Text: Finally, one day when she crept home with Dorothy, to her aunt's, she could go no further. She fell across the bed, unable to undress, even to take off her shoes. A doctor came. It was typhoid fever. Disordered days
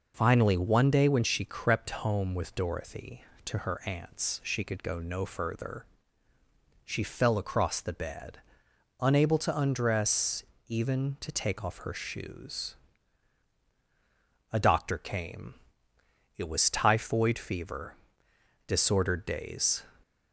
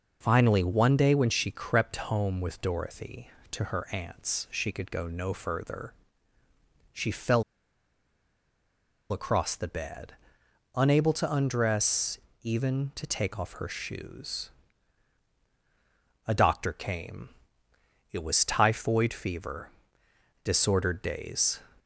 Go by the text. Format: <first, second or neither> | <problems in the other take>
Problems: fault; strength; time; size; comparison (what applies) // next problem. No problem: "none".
first | pauses between "fell" and "across"; strong; at 7.4 s; 1.6 s long